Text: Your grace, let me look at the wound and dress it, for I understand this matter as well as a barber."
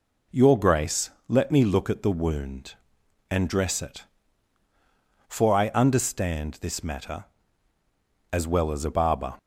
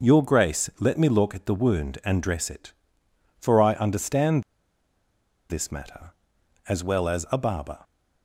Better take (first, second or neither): first